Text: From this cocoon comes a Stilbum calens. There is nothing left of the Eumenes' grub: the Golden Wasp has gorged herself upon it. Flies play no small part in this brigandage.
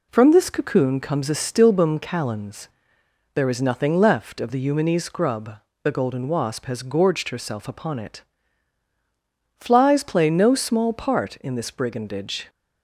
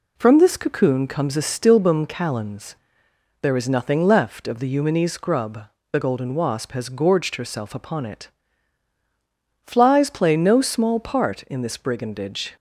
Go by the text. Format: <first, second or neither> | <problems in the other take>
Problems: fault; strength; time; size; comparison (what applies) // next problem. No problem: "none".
neither | none